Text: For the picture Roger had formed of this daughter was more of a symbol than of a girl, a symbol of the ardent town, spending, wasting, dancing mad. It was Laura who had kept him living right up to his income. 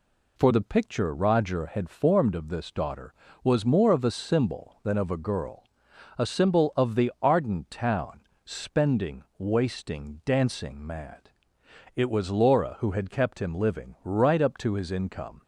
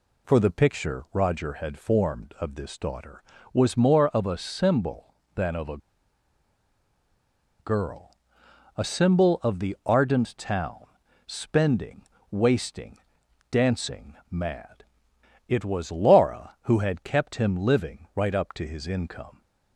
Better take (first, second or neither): first